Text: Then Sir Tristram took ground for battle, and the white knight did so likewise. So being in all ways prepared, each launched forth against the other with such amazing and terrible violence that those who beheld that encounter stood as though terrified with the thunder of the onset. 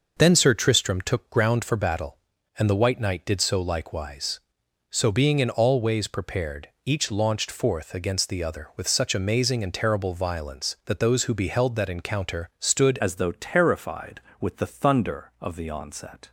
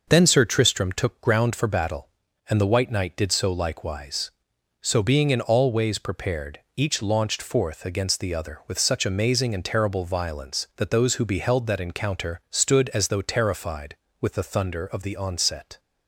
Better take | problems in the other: second | starts louder than the rest; noticeable; until 1.1 s; 6 dB; noticeable in the second // changes voice at "as"; from 12.9 s on; 3.4 s long

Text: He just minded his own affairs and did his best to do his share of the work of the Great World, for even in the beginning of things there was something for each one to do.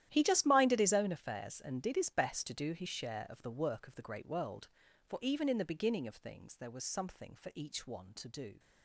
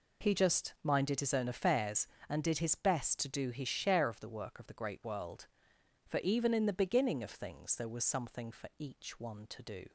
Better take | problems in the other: second | gets quieter; strong; throughout; 16.5 dB

